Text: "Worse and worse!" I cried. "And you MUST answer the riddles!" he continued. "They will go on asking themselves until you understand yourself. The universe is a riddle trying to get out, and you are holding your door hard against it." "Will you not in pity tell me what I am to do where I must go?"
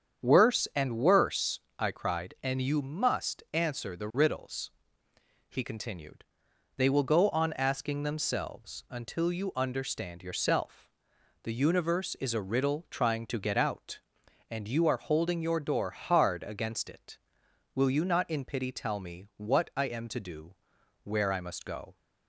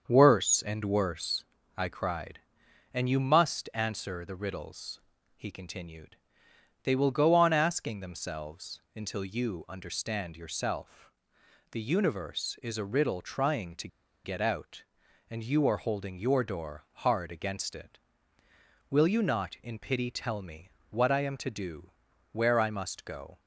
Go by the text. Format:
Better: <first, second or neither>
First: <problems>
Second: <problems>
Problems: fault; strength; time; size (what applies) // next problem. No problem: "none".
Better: first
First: starts louder than the rest; strong; until 1.3 s; 8 dB // pauses between "do" and "where"; noticeable; at 20.5 s; 0.48 s long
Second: starts louder than the rest; until 1.0 s; 7 dB // pauses between "to" and "get"; at 13.8 s; 0.37 s long // pauses between "me" and "what"; slight; at 20.6 s; 0.20 s long // pauses between "do" and "where"; at 21.9 s; 0.40 s long